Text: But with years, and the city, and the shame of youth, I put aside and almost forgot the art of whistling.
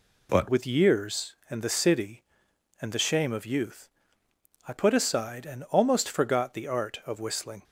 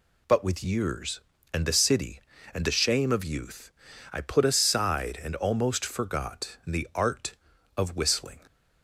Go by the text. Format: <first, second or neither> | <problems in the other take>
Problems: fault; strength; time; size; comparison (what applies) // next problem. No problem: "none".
second | changes voice at "with"; from 0.4 s on; 7.2 s long